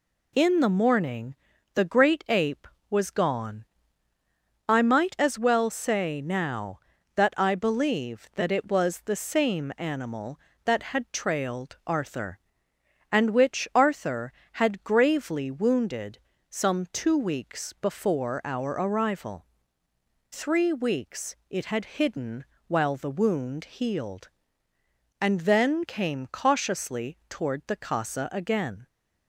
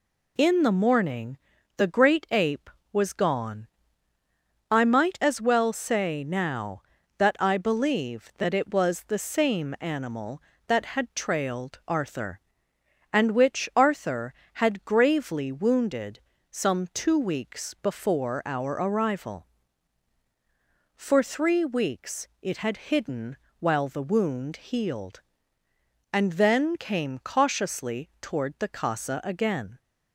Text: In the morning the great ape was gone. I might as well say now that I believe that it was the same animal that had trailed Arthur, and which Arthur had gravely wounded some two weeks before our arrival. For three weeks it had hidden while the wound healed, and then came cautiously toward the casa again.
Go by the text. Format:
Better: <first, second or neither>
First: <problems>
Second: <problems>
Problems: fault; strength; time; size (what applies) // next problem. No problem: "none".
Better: second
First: pauses between "morning" and "the"; at 1.3 s; 0.38 s long // pauses between "wounded" and "some"; slight; at 16.1 s; 0.32 s long // skips "For"; at 19.8 s // pauses between "hidden" and "while"; slight; at 22.4 s; 0.22 s long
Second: pauses between "morning" and "the"; at 1.3 s; 0.38 s long // pauses between "wounded" and "some"; slight; at 16.1 s; 0.32 s long // pauses between "hidden" and "while"; slight; at 23.3 s; 0.22 s long